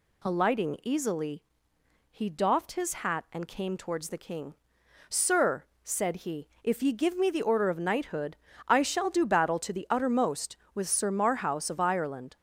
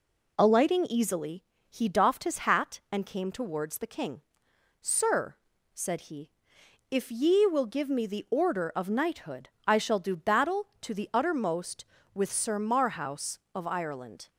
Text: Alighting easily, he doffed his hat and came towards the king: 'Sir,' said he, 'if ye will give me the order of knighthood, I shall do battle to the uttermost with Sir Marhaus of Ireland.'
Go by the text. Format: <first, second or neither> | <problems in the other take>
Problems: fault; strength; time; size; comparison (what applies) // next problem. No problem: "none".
second | skips "will"; at 6.9 s